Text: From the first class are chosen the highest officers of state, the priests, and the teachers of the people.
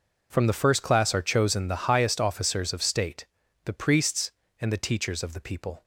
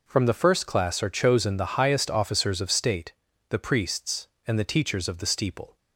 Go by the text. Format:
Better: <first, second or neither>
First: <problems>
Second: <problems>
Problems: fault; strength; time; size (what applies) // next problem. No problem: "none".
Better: first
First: none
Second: says "steeple" for "people"; at 5.2 s